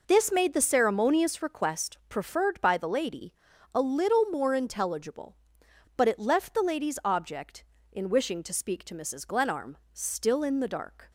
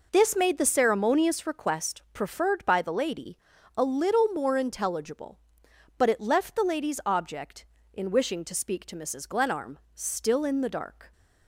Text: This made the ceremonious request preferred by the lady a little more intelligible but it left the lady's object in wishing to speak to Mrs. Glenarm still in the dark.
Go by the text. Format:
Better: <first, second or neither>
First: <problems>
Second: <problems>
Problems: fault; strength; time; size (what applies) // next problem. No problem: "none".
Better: neither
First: pauses between "lady" and "a"; at 3.3 s; 0.40 s long // pauses between "Glenarm" and "still"; slight; at 9.7 s; 0.16 s long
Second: pauses between "lady" and "a"; at 3.3 s; 0.38 s long // pauses between "Glenarm" and "still"; slight; at 9.7 s; 0.16 s long